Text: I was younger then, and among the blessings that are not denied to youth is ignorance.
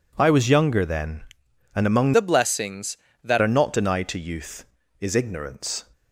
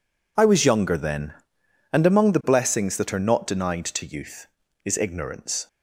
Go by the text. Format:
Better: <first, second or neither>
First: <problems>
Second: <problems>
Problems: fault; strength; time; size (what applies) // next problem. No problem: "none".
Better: second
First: changes voice from "the" to "that"; from 2.1 to 3.3 s; 1.2 s long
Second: none